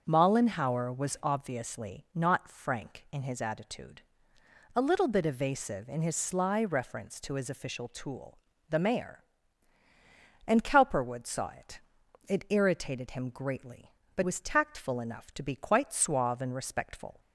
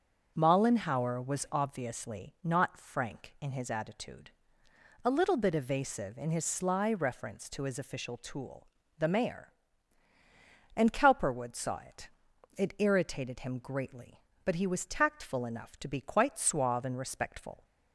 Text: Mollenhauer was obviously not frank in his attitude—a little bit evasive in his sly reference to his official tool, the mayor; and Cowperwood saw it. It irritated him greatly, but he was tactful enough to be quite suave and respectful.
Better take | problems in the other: second | starts louder than the rest; until 1.0 s; 6.5 dB; also in the second // skips "he"; at 14.2 s

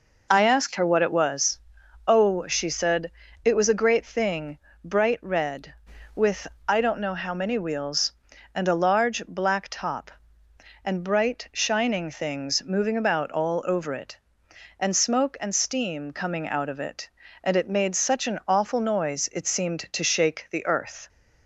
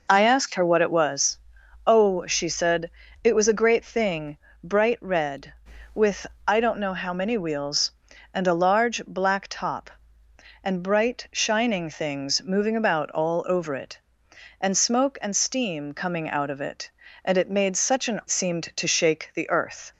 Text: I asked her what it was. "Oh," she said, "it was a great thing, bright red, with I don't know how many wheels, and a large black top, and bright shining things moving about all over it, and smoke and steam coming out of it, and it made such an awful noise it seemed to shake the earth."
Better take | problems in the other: first | pauses between "with" and "I"; slight; at 6.2 s; 0.22 s long; slight in the first // skips "awful noise it"; at 18.2 s

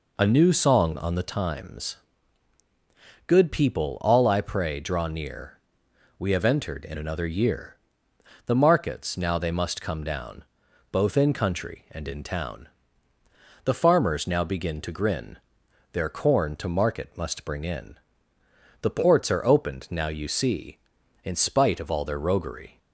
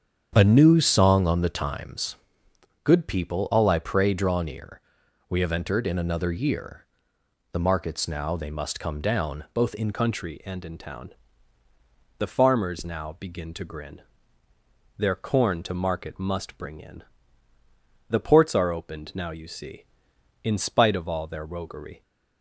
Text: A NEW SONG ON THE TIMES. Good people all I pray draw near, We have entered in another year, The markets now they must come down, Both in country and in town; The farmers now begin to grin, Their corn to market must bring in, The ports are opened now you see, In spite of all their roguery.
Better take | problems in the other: first | starts louder than the rest; strong; until 1.3 s; 8 dB // changes voice at "country"; from 9.9 s on; 12.1 s long

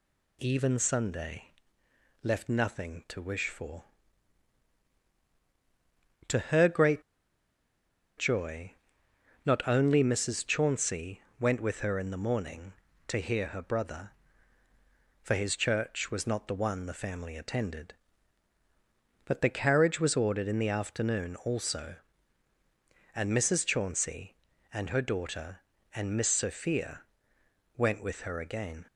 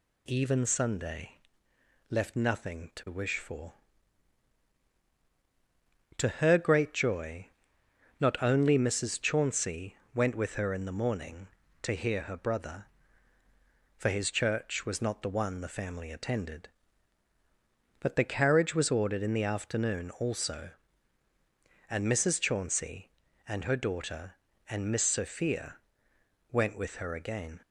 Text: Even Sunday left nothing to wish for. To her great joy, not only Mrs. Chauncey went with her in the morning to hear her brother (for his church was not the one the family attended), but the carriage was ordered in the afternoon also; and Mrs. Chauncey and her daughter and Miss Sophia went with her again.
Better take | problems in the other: second | pauses between "Sunday" and "left"; noticeable; at 1.4 s; 0.74 s long; noticeable in the second // pauses between "great" and "joy"; at 7.0 s; 1.1 s long // pauses between "Chauncey" and "went"; slight; at 11.2 s; 0.18 s long; slight in the second // pauses between "Sophia" and "went"; noticeable; at 27.0 s; 0.74 s long; noticeable in the second

